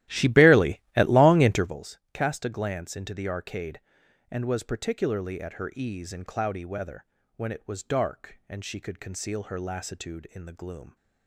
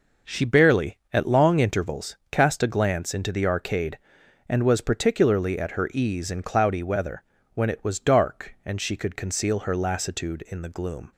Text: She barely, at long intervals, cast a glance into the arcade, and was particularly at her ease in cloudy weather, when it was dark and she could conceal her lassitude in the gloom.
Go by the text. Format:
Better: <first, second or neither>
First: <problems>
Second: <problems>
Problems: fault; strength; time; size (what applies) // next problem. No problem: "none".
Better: second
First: starts louder than the rest; strong; until 1.7 s; 15 dB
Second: none